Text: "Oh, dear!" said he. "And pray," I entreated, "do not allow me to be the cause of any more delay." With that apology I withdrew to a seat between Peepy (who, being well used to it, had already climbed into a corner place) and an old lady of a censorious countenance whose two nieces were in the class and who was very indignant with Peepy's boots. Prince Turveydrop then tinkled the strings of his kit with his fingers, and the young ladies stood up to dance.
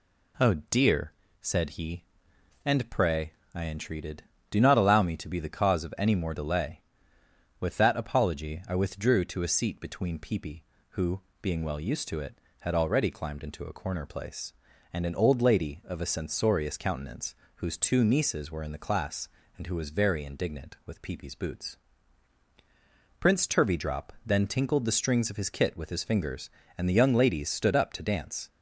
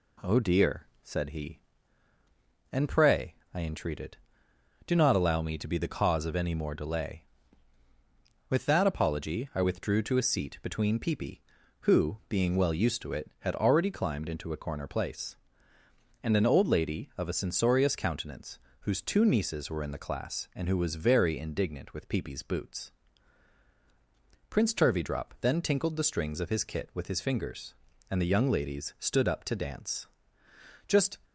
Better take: first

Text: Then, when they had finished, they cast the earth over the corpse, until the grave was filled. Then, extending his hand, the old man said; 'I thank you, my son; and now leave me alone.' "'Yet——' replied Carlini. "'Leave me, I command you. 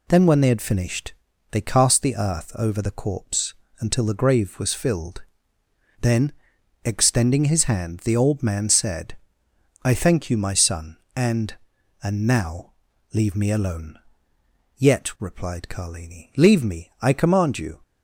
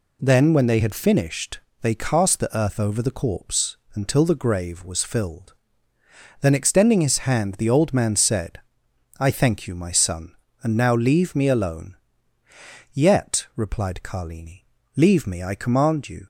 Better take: second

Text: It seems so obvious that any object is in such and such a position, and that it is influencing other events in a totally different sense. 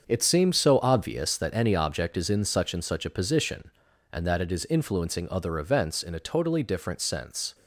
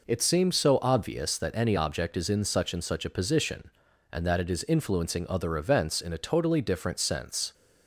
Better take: second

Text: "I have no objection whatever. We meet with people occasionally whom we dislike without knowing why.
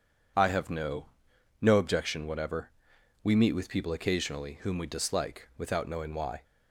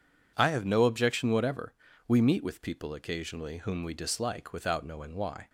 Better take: second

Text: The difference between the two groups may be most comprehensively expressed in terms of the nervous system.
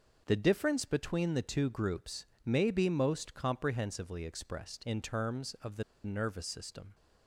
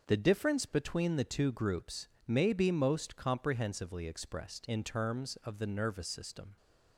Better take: second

